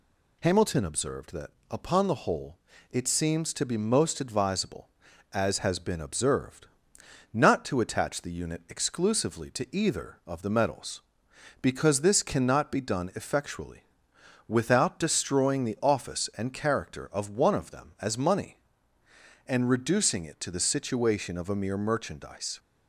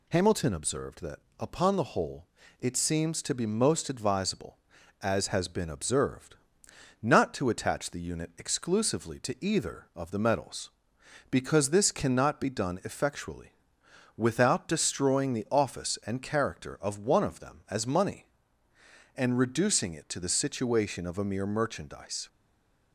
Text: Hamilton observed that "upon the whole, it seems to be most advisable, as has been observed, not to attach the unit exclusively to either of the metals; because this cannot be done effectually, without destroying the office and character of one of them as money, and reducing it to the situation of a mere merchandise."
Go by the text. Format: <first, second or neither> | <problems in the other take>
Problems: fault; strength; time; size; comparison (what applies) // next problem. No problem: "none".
first | pauses between "that" and "upon"; slight; at 1.1 s; 0.20 s long; slight in the first // stays silent after the last word; slight; from 22.2 s on; 0.7 s long